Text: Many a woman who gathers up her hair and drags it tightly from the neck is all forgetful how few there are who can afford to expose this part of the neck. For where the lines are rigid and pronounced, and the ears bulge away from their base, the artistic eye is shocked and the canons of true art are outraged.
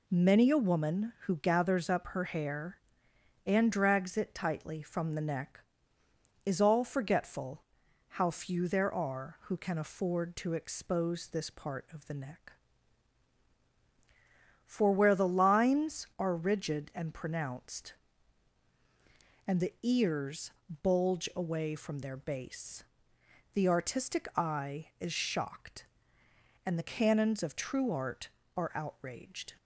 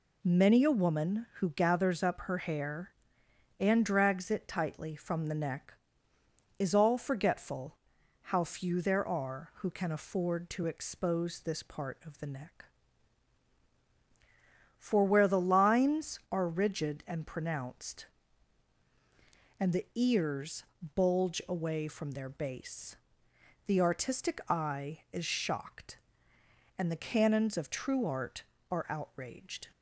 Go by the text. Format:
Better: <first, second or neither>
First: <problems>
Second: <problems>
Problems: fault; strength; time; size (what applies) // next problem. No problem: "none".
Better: neither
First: pauses between "forgetful" and "how"; noticeable; at 7.6 s; 0.48 s long // pauses between "ears" and "bulge"; slight; at 20.5 s; 0.32 s long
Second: pauses between "forgetful" and "how"; noticeable; at 7.7 s; 0.48 s long // pauses between "ears" and "bulge"; slight; at 20.6 s; 0.32 s long